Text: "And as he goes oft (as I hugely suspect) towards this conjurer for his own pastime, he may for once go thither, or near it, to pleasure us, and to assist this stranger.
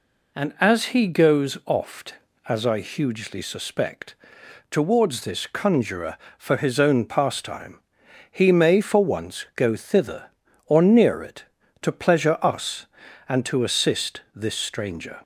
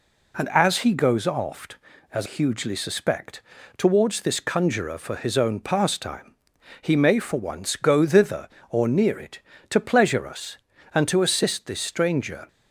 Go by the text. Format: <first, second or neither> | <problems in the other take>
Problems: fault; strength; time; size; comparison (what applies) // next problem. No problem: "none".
first | skips "I"; at 2.2 s